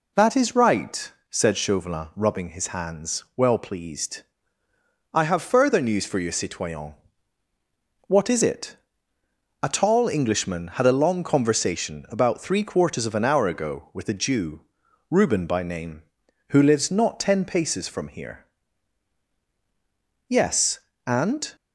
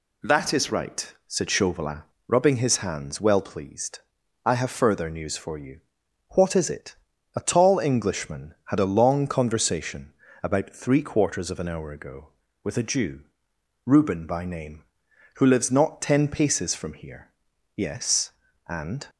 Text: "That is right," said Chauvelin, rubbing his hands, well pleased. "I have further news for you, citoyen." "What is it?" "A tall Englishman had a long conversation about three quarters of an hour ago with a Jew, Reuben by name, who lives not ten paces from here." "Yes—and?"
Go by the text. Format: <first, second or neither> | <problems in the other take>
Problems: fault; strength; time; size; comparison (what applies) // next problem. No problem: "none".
first | skips "citoyen"; at 6.0 s // pauses between "conversation" and "about"; slight; at 10.1 s; 0.30 s long